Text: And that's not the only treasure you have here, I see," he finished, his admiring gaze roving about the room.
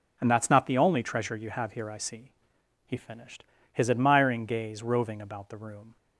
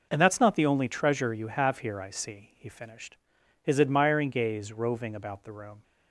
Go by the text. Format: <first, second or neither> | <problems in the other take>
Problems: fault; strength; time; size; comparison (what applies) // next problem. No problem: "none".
neither | none